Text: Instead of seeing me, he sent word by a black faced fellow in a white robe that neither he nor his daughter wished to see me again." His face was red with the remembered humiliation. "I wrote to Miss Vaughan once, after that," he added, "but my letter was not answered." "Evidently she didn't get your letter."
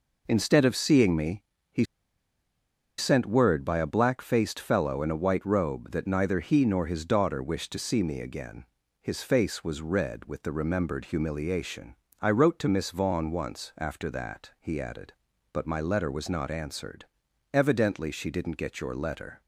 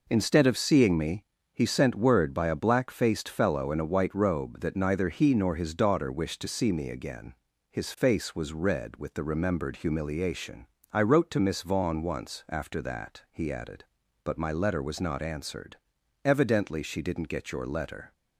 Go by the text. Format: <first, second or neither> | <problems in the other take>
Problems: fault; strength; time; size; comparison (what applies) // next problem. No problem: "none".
second | pauses between "he" and "sent"; at 1.8 s; 1.1 s long